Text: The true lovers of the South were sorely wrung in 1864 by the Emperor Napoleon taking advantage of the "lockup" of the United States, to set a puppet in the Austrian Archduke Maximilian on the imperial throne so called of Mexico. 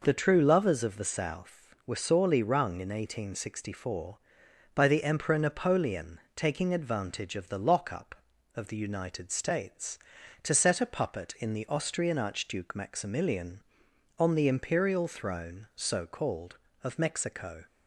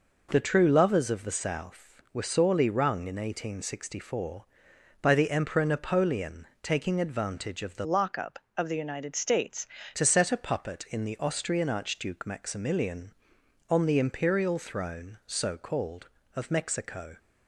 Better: first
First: pauses between "Napoleon" and "taking"; slight; at 6.1 s; 0.16 s long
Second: pauses between "Napoleon" and "taking"; slight; at 6.4 s; 0.16 s long // changes voice from "lockup" to "States"; from 7.8 to 9.6 s; 1.8 s long

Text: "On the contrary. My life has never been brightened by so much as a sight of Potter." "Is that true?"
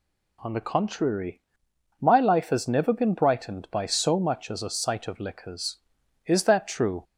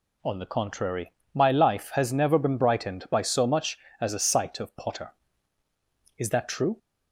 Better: second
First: says "Liquors" for "Potter"; at 5.1 s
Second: none

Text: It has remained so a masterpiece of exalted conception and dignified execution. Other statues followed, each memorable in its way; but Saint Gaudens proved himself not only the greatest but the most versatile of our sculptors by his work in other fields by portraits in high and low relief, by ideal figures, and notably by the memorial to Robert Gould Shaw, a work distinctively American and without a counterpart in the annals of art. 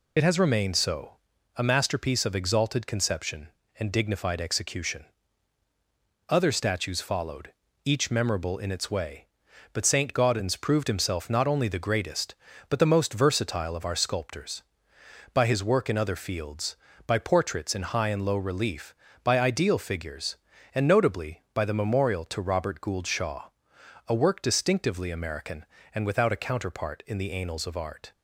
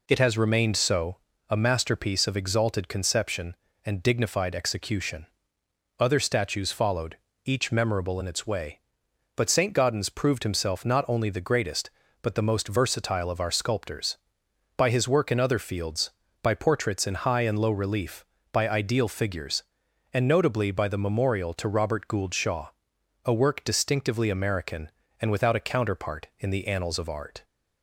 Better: second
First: loses the start of "It"; at 0.1 s; 55 ms // pauses between "so" and "a"; at 1.1 s; 0.42 s long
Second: pauses between "so" and "a"; slight; at 1.1 s; 0.30 s long

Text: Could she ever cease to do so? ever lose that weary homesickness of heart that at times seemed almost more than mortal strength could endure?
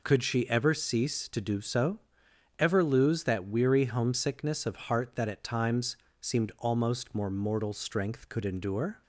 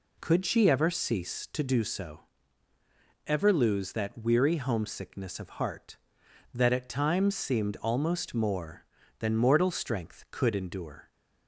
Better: second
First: pauses between "times" and "seemed"; slight; at 5.9 s; 0.24 s long // skips "than"; at 7.2 s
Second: none

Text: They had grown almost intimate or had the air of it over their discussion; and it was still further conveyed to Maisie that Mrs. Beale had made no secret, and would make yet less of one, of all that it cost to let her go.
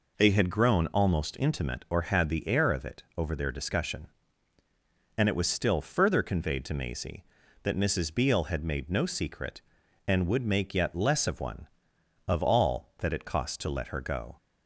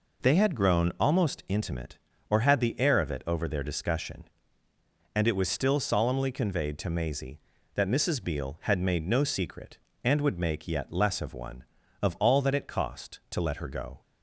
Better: first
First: none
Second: says "solemnly" for "further"; at 5.7 s

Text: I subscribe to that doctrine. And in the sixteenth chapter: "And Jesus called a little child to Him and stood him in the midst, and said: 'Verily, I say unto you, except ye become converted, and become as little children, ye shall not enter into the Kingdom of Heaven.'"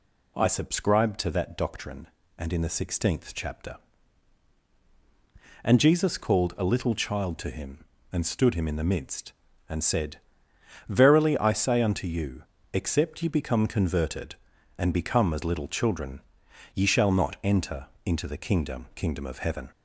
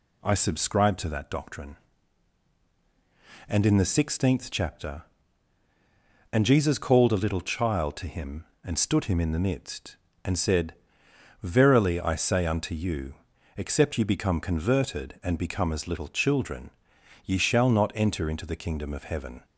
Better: second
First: pauses between "enter" and "into"; slight; at 17.8 s; 0.18 s long // says "Kingdom" twice; at 18.9 s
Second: none

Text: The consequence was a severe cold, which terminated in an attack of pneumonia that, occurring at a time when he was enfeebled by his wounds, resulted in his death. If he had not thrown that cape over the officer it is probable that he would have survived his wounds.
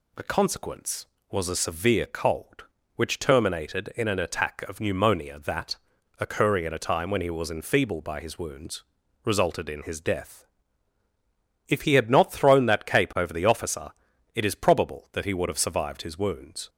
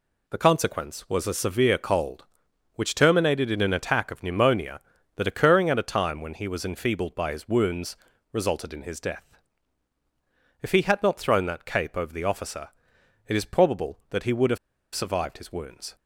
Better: first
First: pauses between "officer" and "it"; at 13.9 s; 0.42 s long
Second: pauses between "officer" and "it"; noticeable; at 12.6 s; 0.60 s long // pauses between "have" and "survived"; at 14.5 s; 0.37 s long

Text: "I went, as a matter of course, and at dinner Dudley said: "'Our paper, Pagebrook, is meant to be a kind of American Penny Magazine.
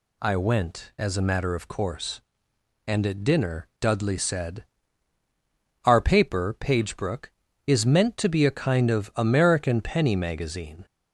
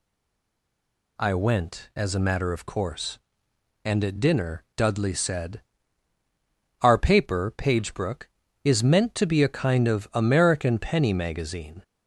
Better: first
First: none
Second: stays silent before the first word; noticeable; until 1.1 s; 1.1 s long

